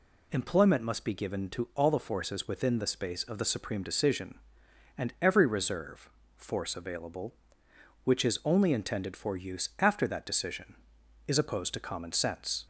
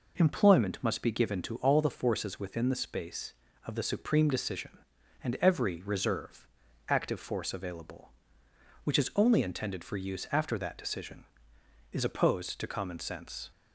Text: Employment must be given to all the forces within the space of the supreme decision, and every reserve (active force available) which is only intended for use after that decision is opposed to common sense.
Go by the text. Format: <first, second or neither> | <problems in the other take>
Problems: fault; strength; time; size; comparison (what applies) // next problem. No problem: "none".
second | skips "active"; at 6.2 s